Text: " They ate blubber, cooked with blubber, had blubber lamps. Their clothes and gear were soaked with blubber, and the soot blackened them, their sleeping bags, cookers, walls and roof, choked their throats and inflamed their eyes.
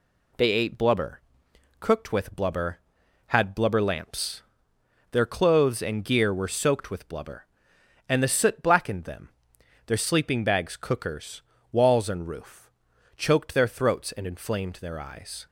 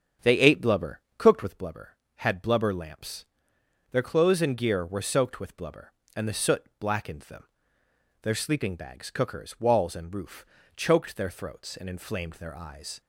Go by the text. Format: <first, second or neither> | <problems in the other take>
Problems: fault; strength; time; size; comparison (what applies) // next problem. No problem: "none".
first | starts louder than the rest; strong; until 1.7 s; 8 dB